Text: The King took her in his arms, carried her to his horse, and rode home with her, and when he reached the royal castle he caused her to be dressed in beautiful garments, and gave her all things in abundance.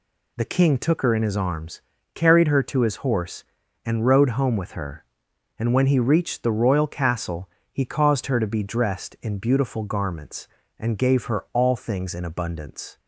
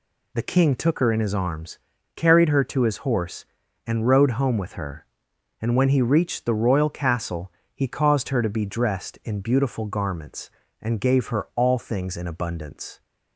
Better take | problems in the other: neither | pauses between "castle" and "he"; slight; the same in both

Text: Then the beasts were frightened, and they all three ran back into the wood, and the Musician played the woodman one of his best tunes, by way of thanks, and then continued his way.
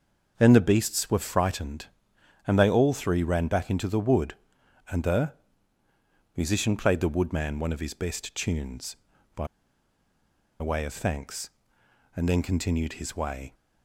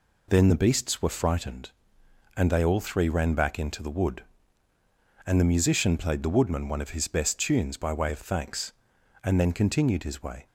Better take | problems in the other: second | pauses between "the" and "Musician"; at 5.3 s; 1.0 s long // pauses between "by" and "way"; at 9.4 s; 1.1 s long

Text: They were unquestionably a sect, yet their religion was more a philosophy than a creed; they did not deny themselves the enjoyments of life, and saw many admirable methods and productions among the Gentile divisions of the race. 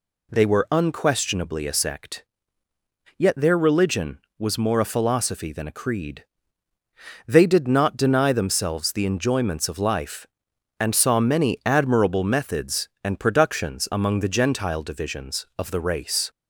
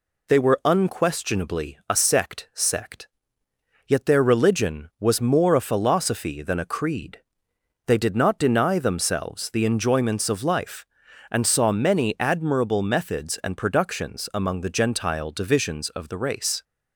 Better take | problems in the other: first | says "sect" twice; at 2.5 s

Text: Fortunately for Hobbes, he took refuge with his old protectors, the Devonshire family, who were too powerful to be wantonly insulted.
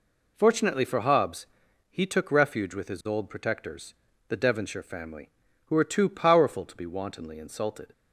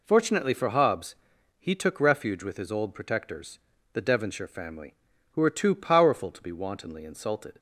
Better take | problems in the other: neither | none

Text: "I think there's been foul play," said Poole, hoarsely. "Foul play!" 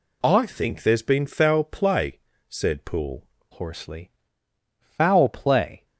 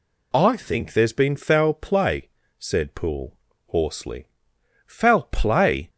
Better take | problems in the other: second | changes voice at "hoarsely"; from 3.5 s on; 2.3 s long

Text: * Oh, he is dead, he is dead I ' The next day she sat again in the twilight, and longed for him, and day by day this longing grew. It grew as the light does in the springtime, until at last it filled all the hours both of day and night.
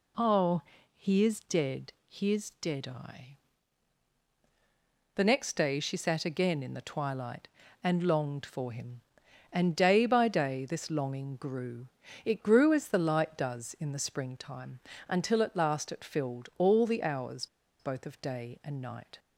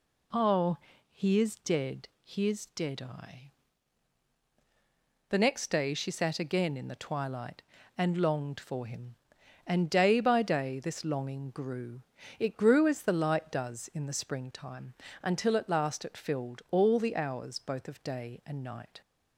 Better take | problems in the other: second | pauses between "hours" and "both"; slight; at 17.4 s; 0.33 s long

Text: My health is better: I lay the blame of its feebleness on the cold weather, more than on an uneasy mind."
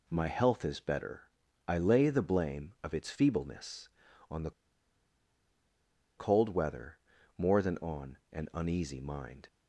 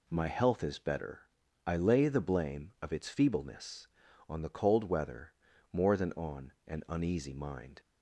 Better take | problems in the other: second | pauses between "the" and "cold"; strong; at 4.5 s; 1.6 s long // pauses between "on" and "an"; slight; at 8.1 s; 0.16 s long; slight in the second

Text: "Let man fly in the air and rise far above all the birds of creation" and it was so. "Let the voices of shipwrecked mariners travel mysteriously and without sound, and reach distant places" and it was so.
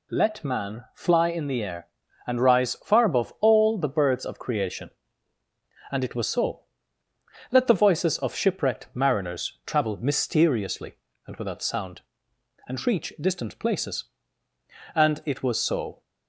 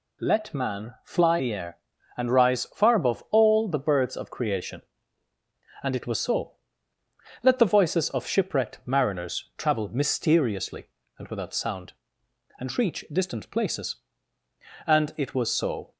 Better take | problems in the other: first | skips "in"; at 1.3 s

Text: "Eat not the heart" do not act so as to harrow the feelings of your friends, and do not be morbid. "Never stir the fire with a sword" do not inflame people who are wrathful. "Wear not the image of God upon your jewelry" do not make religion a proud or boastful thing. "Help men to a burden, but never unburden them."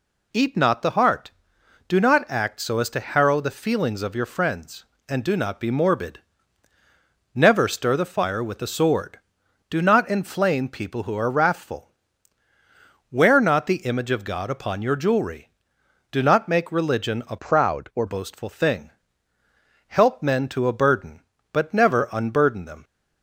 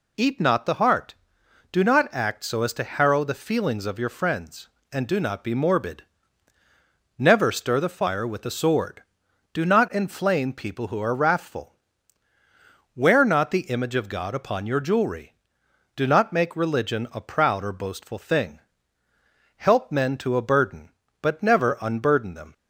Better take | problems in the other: second | changes voice from "proud" to "or"; from 17.3 to 18.0 s; 0.7 s long

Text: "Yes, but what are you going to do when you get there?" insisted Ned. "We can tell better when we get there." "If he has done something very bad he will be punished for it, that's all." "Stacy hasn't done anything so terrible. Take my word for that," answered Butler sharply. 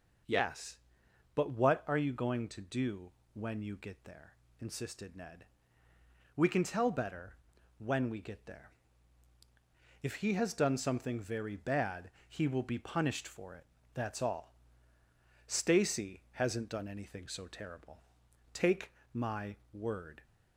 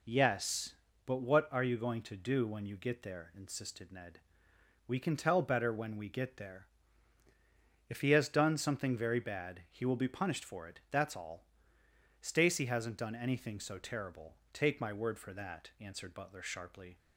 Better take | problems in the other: second | pauses between "do" and "when"; slight; at 3.1 s; 0.22 s long // pauses between "better" and "when"; at 7.3 s; 0.42 s long // pauses between "bad" and "he"; slight; at 12.0 s; 0.18 s long // pauses between "Take" and "my"; slight; at 18.9 s; 0.22 s long // stops before "for that answered Butler sharply"; at 20.2 s

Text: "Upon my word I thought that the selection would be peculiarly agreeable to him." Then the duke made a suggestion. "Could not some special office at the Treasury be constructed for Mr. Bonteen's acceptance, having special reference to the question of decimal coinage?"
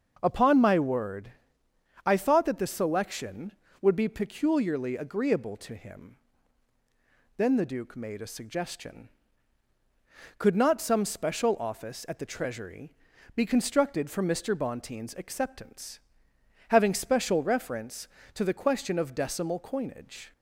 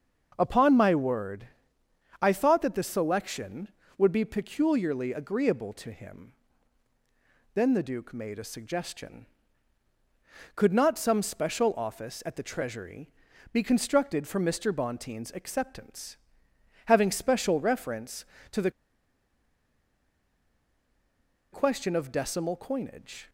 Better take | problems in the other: first | starts louder than the rest; until 1.3 s; 6.5 dB; also in the first // pauses between "word" and "I"; noticeable; at 1.4 s; 0.74 s long; noticeable in the first // pauses between "Treasury" and "be"; at 13.1 s; 0.40 s long; also in the first // pauses between "the" and "question"; strong; at 18.7 s; 2.8 s long

